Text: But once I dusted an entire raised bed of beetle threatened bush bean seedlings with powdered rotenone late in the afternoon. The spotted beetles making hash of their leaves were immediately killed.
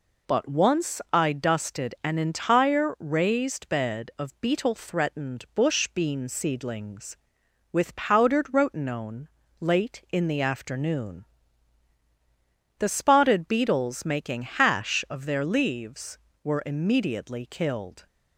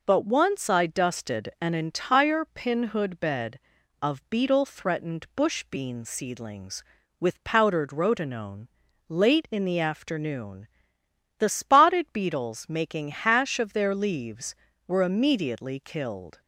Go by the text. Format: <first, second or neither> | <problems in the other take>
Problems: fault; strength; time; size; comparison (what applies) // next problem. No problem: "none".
first | says "pinhood" for "raised"; at 2.4 s // pauses between "rotenone" and "late"; at 8.6 s; 0.42 s long; slight in the first